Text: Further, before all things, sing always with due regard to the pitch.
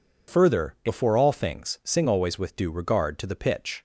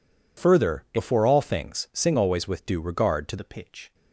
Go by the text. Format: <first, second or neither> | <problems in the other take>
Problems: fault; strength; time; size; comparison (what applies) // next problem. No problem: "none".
first | changes voice at "the"; from 3.3 s on; 0.6 s long